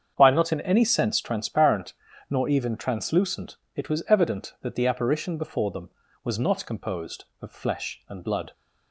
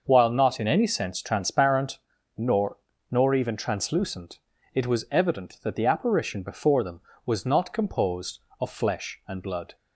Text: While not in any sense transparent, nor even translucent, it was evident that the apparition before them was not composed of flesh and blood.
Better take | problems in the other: first | starts louder than the rest; until 1.0 s; 6.5 dB; strong in the first // says "nor" twice; at 3.0 s

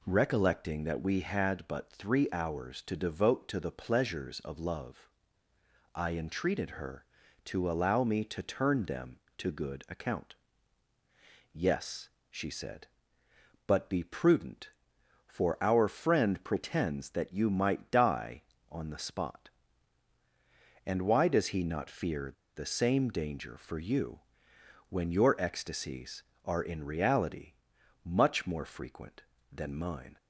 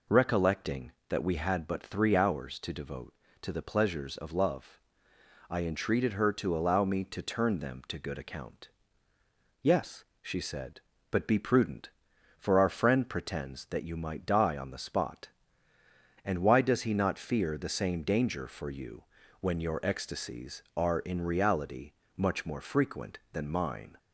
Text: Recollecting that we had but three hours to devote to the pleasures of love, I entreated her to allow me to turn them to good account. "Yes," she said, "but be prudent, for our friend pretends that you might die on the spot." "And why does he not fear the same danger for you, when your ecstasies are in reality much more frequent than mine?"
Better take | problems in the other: second | pauses between "fear" and "the"; slight; at 22.3 s; 0.23 s long // pauses between "reality" and "much"; noticeable; at 27.5 s; 0.50 s long; slight in the second

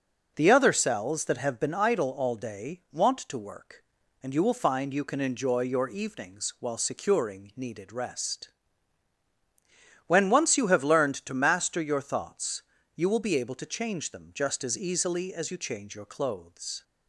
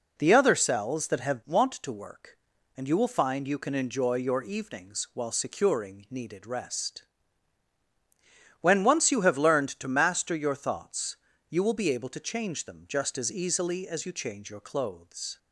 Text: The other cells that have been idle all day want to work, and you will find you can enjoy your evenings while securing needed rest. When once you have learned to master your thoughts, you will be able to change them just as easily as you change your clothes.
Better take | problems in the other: first | skips "been idle all day"; at 1.4 s

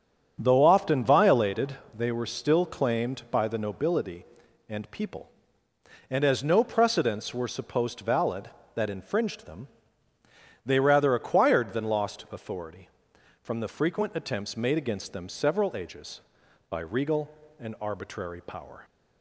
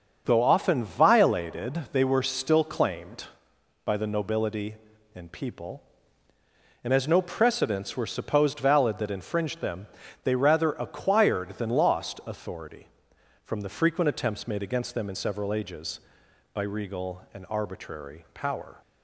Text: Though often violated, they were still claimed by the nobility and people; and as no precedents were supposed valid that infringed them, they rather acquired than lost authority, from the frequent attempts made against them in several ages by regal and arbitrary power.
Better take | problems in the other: second | starts louder than the rest; until 1.4 s; 7 dB; also in the second // skips "in"; at 15.2 s

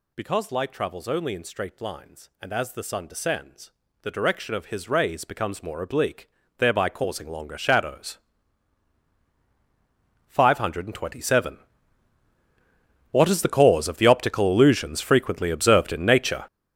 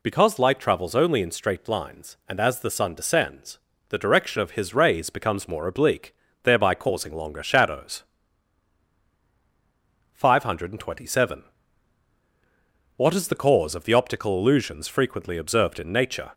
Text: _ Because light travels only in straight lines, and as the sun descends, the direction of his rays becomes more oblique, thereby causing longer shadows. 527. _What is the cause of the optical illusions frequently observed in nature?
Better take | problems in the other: second | gets louder; strong; throughout; 12.5 dB

